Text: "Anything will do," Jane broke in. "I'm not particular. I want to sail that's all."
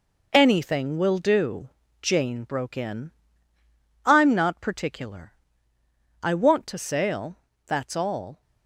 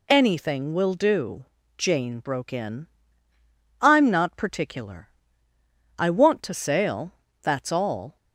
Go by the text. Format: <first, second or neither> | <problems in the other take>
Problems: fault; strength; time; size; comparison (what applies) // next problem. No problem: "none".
second | gets quieter; throughout; 6.5 dB // pauses between "sail" and "that's"; slight; at 7.3 s; 0.30 s long; slight in the second